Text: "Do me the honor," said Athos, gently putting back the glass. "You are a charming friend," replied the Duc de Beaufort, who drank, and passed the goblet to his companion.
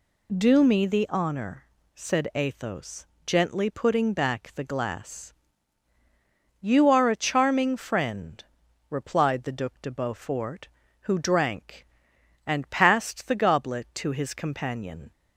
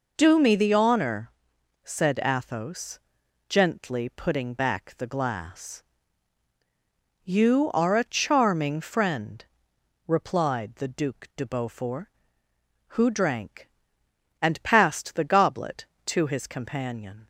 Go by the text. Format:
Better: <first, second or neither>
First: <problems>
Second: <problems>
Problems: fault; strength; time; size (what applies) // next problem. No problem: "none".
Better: neither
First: none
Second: none